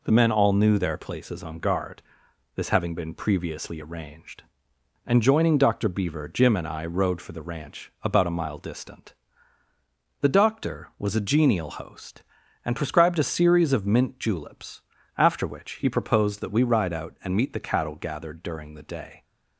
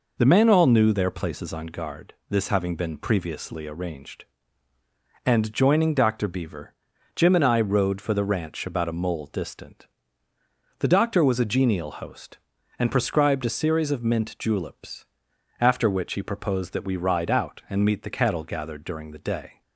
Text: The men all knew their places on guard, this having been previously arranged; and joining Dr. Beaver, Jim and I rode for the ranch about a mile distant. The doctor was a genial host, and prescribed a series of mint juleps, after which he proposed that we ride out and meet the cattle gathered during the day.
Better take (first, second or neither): first